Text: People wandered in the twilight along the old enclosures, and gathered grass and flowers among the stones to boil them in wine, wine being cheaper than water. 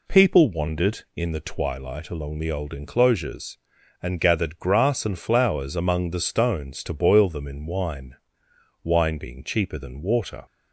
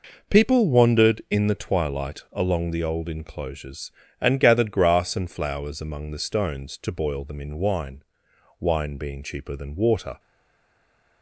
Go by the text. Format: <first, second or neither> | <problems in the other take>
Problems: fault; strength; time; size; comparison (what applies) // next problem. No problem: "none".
first | stays silent after the last word; from 10.1 s on; 1.1 s long